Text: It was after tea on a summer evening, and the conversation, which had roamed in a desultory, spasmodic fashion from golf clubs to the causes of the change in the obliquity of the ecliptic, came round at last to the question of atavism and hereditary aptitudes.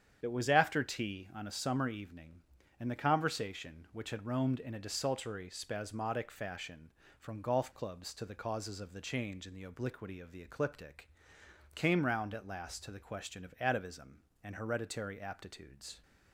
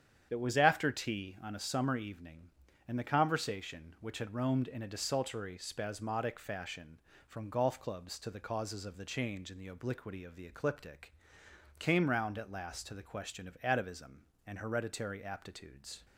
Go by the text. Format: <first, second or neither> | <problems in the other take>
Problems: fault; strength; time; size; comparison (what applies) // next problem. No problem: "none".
neither | starts louder than the rest; strong; the same in both